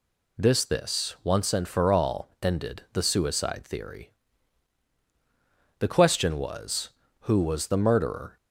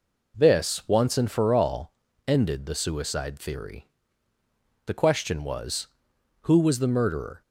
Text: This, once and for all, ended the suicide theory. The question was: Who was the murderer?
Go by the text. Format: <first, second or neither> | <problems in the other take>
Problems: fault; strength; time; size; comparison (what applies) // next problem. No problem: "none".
second | says "This" twice; at 0.6 s